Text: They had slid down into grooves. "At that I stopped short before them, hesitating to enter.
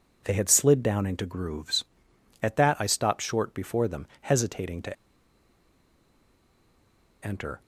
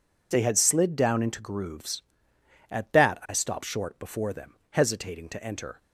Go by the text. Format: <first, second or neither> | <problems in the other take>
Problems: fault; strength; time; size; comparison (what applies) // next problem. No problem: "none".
second | pauses between "to" and "enter"; strong; at 4.9 s; 2.2 s long